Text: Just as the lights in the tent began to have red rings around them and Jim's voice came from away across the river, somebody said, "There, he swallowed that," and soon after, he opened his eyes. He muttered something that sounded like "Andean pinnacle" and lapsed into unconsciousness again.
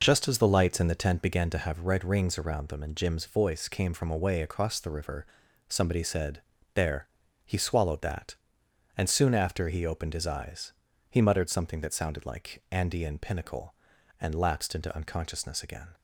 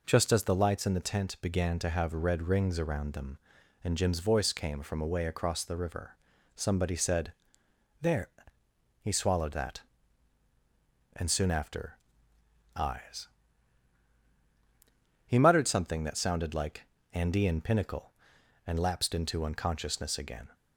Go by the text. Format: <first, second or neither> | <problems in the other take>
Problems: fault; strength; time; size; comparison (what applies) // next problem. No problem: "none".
first | skips "he opened his"; at 12.3 s // pauses between "like" and "Andean"; slight; at 16.8 s; 0.28 s long